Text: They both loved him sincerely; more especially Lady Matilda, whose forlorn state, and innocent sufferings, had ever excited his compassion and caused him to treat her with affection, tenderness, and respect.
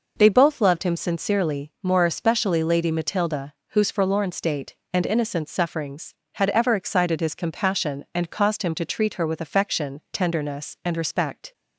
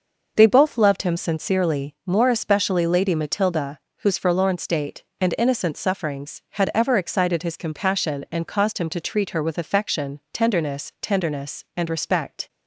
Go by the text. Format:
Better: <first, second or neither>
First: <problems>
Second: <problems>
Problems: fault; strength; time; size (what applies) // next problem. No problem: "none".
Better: first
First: none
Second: says "tenderness" twice; at 11.0 s